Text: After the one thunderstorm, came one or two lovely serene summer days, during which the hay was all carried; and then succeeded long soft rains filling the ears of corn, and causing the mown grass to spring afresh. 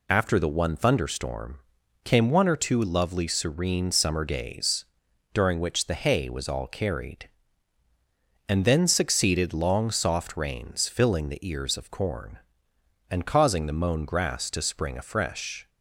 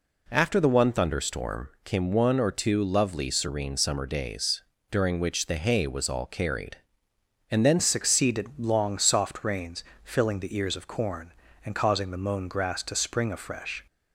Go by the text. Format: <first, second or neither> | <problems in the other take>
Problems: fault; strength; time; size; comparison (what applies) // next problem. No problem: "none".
first | changes voice at "succeeded"; from 7.7 s on; 6.1 s long // pauses between "rains" and "filling"; slight; at 9.8 s; 0.18 s long